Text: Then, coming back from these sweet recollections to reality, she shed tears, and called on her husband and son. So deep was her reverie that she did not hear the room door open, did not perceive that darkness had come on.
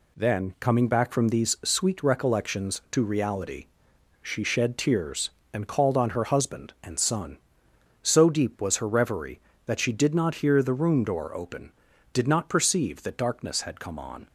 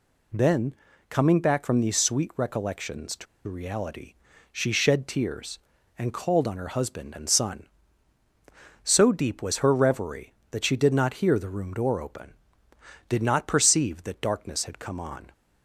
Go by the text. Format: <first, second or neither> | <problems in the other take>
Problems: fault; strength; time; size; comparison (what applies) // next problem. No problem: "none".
first | pauses between "to" and "reality"; slight; at 3.2 s; 0.22 s long